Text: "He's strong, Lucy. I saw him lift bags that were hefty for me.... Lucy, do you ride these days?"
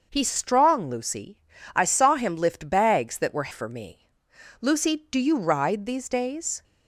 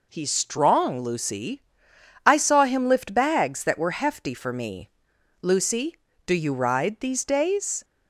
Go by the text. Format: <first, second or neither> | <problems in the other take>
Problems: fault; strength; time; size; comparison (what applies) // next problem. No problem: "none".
second | starts louder than the rest; until 1.1 s; 6.5 dB // skips "hefty"; at 3.5 s